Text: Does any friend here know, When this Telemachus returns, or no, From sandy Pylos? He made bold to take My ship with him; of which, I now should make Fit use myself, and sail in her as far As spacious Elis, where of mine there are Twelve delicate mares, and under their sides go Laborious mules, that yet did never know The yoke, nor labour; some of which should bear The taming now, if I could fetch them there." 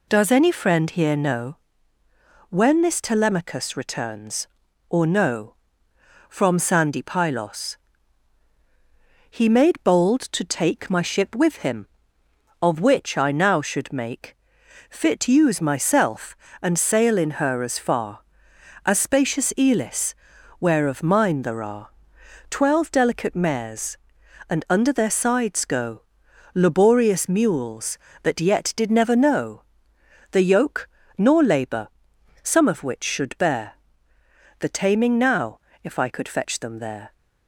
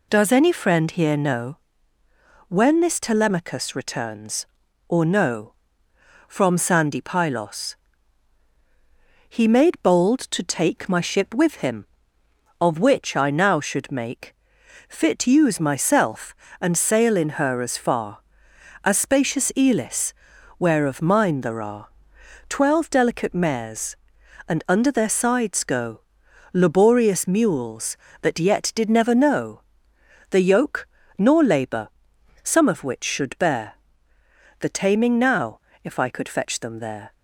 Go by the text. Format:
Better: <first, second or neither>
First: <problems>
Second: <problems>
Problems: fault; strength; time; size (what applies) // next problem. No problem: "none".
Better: neither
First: pauses between "make" and "Fit"; noticeable; at 14.3 s; 0.54 s long // pauses between "are" and "Twelve"; noticeable; at 21.8 s; 0.58 s long // pauses between "go" and "Laborious"; noticeable; at 26.0 s; 0.50 s long // pauses between "know" and "The"; noticeable; at 29.6 s; 0.64 s long // pauses between "bear" and "The"; noticeable; at 33.7 s; 0.80 s long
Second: pauses between "make" and "Fit"; noticeable; at 14.3 s; 0.54 s long // pauses between "are" and "Twelve"; noticeable; at 21.8 s; 0.58 s long // pauses between "go" and "Laborious"; noticeable; at 26.0 s; 0.50 s long // pauses between "know" and "The"; noticeable; at 29.6 s; 0.64 s long // pauses between "bear" and "The"; noticeable; at 33.7 s; 0.80 s long